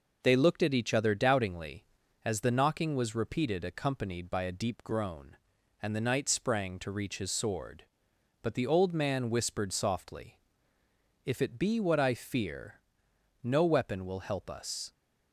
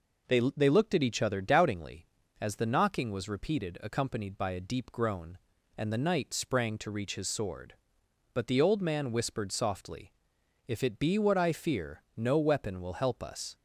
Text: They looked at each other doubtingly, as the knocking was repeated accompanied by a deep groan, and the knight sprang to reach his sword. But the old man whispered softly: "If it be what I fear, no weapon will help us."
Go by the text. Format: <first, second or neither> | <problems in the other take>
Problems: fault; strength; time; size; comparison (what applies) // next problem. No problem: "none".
first | says "They" twice; at 0.5 s